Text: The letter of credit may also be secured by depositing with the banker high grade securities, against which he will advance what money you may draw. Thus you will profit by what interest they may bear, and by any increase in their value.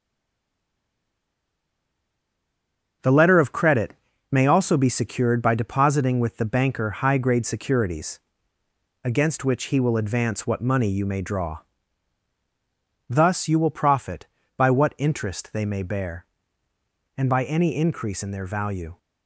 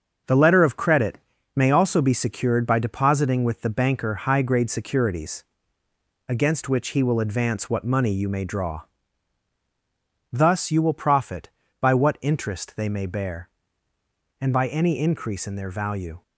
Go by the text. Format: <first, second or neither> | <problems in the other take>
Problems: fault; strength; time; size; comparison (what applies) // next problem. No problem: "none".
second | stays silent before the first word; strong; until 3.0 s; 3.0 s long // starts louder than the rest; until 4.3 s; 6.5 dB; also in the second // pauses between "credit" and "may"; slight; at 3.9 s; 0.36 s long; slight in the second